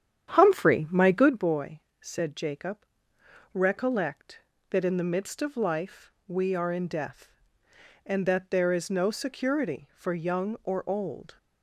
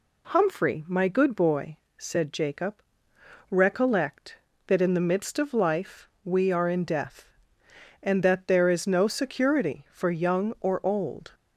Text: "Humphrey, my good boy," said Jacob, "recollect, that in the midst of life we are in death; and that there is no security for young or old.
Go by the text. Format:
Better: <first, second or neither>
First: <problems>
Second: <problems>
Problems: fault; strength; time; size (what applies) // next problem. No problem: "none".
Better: second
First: starts louder than the rest; strong; until 1.4 s; 9.5 dB // pauses between "life" and "we"; slight; at 6.1 s; 0.16 s long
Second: pauses between "life" and "we"; slight; at 6.0 s; 0.16 s long